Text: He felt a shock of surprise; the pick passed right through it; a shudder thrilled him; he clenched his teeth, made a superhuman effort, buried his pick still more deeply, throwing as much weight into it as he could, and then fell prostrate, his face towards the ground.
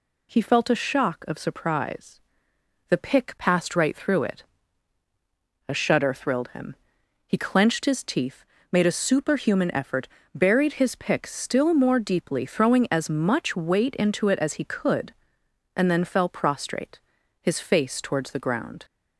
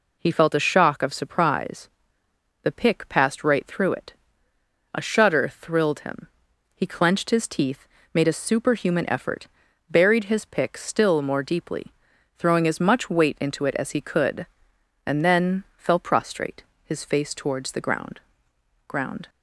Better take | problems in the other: first | says "ground" twice; at 18.8 s

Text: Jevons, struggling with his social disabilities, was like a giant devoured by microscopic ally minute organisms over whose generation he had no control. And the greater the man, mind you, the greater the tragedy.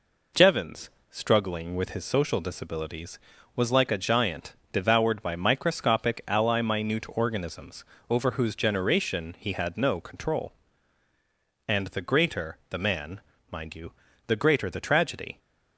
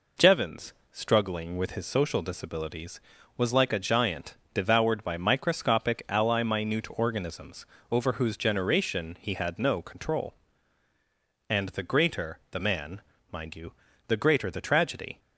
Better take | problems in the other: neither | pauses between "giant" and "devoured"; slight; the same in both // pauses between "organisms" and "over"; slight; the same in both

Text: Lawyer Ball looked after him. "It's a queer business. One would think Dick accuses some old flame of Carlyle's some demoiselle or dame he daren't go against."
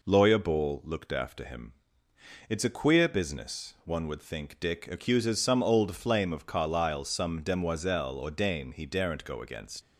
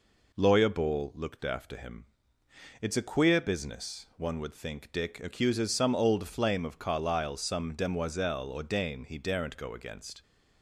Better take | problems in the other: second | leaves "against" unfinished; at 9.8 s; 70 ms

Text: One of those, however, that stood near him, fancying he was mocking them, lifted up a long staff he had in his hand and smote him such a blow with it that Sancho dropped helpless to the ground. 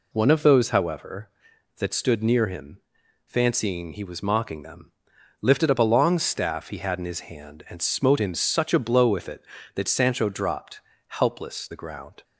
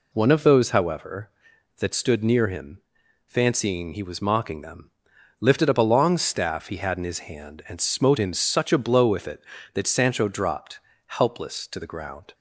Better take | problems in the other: second | pauses between "dropped" and "helpless"; slight; at 10.8 s; 0.26 s long; slight in the second // skips "to"; at 11.6 s

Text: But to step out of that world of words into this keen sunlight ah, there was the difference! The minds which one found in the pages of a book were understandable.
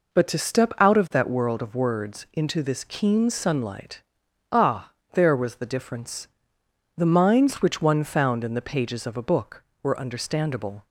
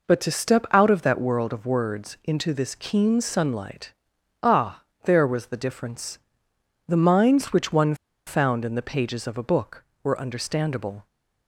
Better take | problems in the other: first | pauses between "sunlight" and "ah"; noticeable; at 3.9 s; 0.50 s long; noticeable in the first // pauses between "one" and "found"; slight; at 7.9 s; 0.32 s long

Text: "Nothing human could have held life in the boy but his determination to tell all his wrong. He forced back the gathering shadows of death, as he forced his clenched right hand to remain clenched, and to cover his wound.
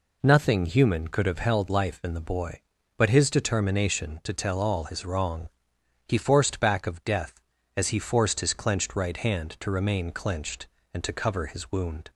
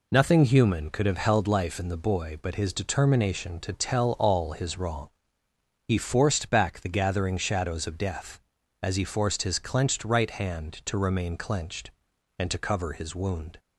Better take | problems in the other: second | skips "the gathering shadows"; at 6.8 s

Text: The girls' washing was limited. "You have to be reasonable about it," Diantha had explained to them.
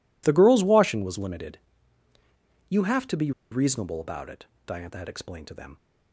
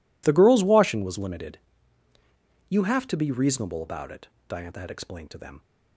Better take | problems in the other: second | pauses between "be" and "reasonable"; slight; at 3.3 s; 0.21 s long

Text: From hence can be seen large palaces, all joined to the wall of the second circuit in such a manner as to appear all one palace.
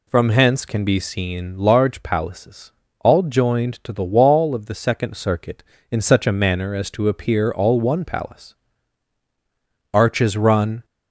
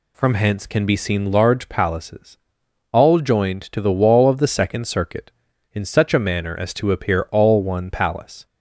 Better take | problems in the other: second | goes on to say "Arches run"; noticeable; from 9.9 s on; 0.92 s long

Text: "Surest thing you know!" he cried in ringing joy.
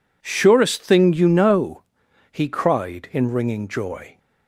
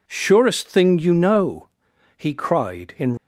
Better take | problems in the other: first | stops before "ringing joy"; at 3.1 s

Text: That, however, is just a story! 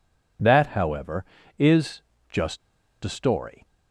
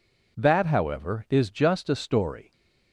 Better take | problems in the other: second | pauses between "is" and "just"; slight; at 2.0 s; 0.30 s long // pauses between "just" and "a"; at 2.6 s; 0.44 s long

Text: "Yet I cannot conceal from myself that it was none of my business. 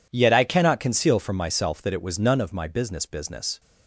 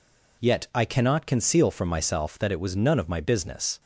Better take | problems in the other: second | says "business" twice; at 3.0 s

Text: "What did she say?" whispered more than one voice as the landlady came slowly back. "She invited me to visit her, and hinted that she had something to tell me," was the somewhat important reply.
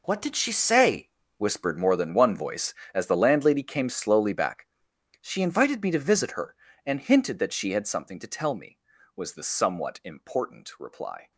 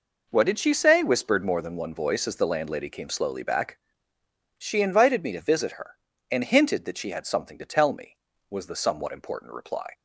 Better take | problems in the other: second | gets quieter; strong; throughout; 14.5 dB

